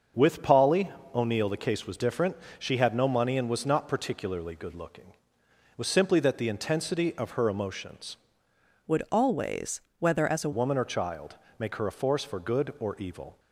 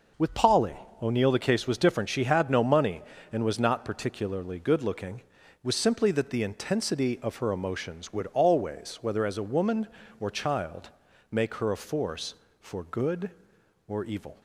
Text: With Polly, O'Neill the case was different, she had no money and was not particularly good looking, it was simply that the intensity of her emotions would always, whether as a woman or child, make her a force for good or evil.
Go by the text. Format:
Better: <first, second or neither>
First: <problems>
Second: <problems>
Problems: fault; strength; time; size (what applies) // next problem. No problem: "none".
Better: second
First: starts louder than the rest; until 1.3 s; 7 dB // changes voice from "would" to "a"; from 8.8 to 10.5 s; 1.7 s long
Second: starts louder than the rest; noticeable; until 1.4 s; 6 dB